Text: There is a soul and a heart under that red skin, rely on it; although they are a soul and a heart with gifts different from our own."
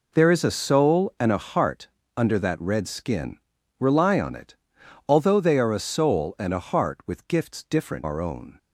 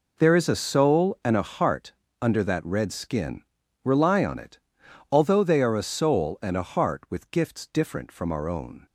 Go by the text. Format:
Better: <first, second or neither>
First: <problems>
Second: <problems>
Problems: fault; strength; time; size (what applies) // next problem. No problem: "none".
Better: second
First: pauses between "heart" and "under"; slight; at 1.8 s; 0.30 s long // skips "from"; at 8.0 s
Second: pauses between "heart" and "under"; slight; at 1.9 s; 0.30 s long